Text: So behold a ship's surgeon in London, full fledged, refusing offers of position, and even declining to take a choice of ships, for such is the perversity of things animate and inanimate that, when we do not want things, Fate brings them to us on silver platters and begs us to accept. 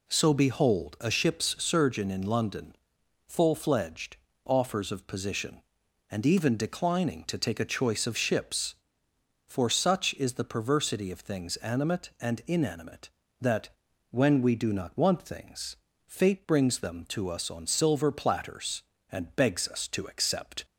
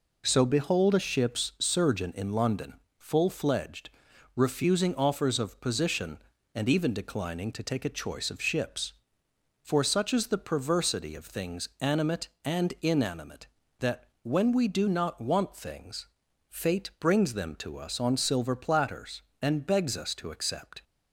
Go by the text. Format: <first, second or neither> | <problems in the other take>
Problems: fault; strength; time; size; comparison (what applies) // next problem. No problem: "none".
second | skips "refusing"; at 4.3 s